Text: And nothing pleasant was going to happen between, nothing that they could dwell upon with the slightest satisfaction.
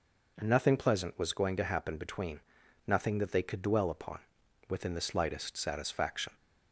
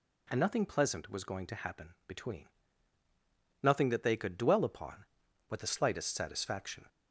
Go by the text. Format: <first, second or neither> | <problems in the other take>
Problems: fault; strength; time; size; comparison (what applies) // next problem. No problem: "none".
second | says "within" for "with"; at 4.6 s